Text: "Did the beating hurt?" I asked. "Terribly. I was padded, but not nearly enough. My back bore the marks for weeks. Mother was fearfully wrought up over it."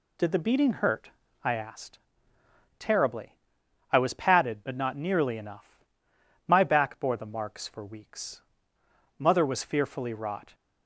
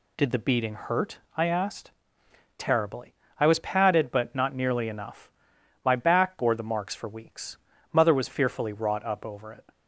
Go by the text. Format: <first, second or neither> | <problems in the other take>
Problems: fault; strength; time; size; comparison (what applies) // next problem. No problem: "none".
second | stops before "up over it"; at 10.5 s